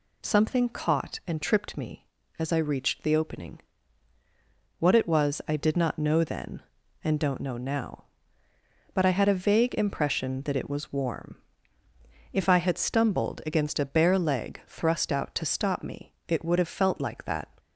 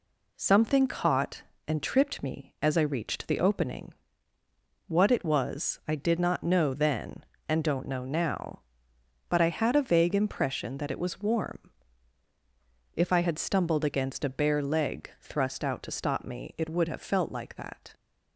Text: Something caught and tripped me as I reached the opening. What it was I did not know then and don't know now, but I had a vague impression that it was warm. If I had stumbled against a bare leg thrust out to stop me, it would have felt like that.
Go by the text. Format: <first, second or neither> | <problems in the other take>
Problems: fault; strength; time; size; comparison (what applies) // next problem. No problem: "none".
neither | none